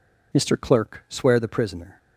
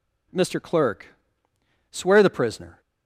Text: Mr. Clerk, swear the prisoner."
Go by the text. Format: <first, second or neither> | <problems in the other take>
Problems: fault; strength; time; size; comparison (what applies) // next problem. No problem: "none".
neither | none